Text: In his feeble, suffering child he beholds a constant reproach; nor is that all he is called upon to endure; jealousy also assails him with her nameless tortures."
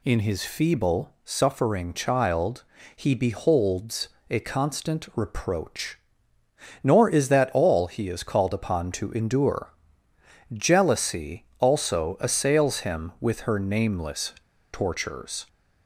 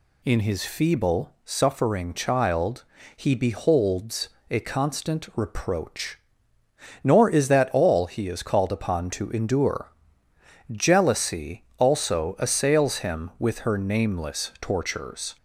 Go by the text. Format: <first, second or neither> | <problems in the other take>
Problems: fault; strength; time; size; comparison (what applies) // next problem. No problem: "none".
second | pauses between "child" and "he"; slight; at 2.6 s; 0.32 s long; slight in the second // pauses between "beholds" and "a"; slight; at 4.0 s; 0.22 s long; slight in the second // pauses between "nameless" and "tortures"; at 14.3 s; 0.39 s long